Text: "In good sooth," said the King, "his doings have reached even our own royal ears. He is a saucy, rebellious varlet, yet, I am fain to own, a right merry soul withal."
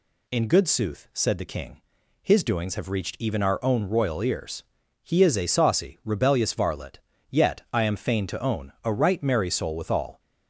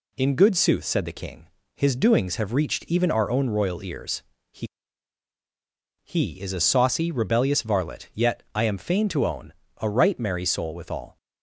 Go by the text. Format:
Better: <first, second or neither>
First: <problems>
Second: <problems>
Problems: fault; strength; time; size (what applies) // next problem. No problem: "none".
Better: first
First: none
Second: says "He" twice; at 6.0 s